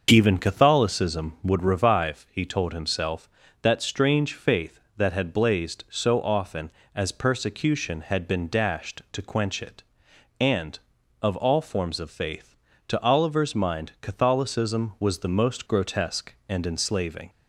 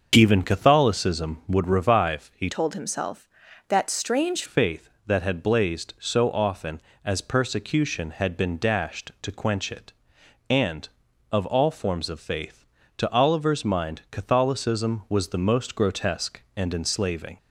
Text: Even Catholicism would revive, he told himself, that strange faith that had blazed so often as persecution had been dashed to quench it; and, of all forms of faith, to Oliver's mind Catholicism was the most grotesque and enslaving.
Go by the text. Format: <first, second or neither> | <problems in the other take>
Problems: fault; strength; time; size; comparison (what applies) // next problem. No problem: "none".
first | starts louder than the rest; noticeable; until 1.1 s; 6 dB // changes voice from "told" to "strange"; from 2.4 to 4.4 s; 2.0 s long